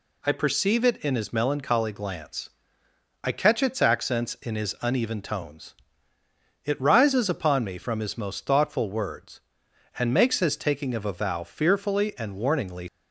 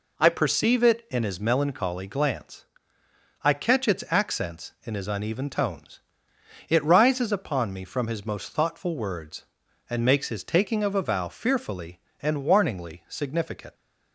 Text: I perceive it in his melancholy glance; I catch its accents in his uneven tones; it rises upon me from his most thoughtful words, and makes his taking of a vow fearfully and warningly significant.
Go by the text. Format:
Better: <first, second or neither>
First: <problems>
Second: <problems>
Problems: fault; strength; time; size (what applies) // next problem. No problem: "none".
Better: second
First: stops before "significant"; at 12.8 s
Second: none